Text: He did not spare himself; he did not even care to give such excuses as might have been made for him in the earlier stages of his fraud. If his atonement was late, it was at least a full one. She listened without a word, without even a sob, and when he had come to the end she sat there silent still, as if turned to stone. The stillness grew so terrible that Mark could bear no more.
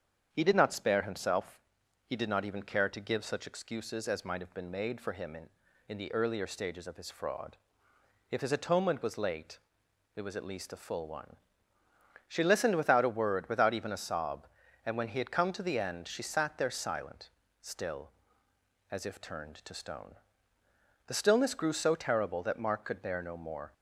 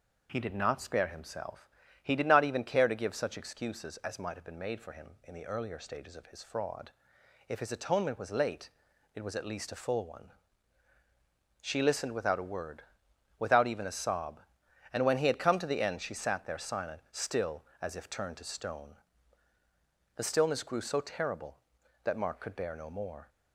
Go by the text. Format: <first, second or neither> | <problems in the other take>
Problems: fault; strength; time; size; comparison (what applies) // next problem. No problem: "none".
second | starts louder than the rest; strong; until 1.3 s; 7.5 dB // says "in" twice; at 5.8 s // pauses between "silent" and "still"; slight; at 17.2 s; 0.32 s long